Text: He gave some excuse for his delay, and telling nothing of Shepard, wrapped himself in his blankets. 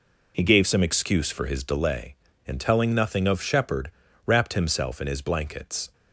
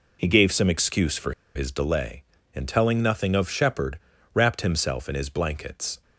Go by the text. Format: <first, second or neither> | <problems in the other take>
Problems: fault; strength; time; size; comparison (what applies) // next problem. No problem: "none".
first | pauses between "for" and "his"; slight; at 1.3 s; 0.23 s long